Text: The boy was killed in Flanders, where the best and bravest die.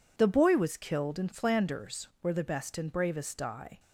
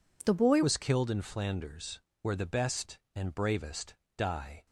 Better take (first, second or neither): first